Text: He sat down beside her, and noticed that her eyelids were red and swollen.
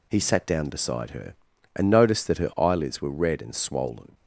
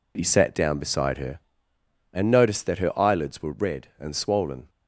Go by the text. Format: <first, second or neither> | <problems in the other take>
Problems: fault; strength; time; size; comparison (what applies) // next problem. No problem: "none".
neither | none